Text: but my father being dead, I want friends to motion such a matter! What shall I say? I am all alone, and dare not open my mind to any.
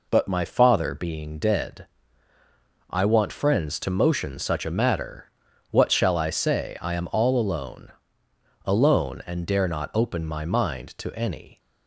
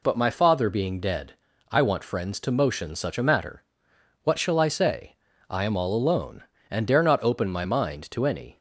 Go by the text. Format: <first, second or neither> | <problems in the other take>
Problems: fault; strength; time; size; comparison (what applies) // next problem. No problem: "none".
second | says "alone" twice; at 8.6 s